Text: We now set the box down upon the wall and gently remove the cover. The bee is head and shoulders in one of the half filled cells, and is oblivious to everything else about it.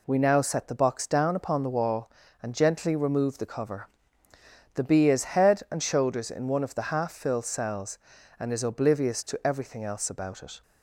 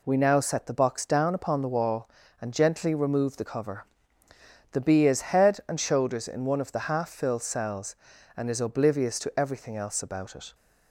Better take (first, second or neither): neither